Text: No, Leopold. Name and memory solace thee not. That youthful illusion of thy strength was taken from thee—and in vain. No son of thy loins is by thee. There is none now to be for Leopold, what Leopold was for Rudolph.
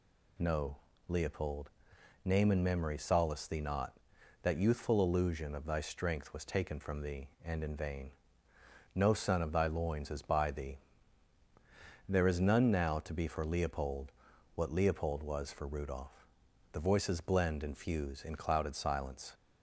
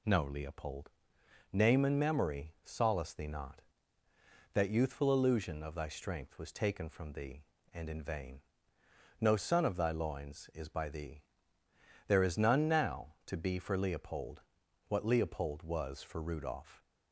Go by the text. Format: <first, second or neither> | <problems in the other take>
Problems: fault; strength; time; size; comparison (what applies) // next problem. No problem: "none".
second | goes on to say "The voices blend and fuse in clouded silence"; strong; from 16.7 s on; 2.6 s long